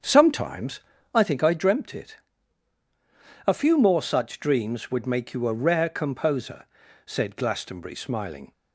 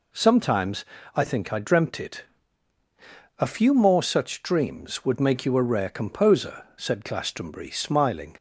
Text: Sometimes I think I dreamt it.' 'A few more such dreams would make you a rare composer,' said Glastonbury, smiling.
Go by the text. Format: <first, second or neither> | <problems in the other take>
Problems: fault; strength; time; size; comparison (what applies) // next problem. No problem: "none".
second | starts louder than the rest; strong; until 1.3 s; 7.5 dB // pauses between "Sometimes" and "I"; slight; at 0.7 s; 0.34 s long; slight in the second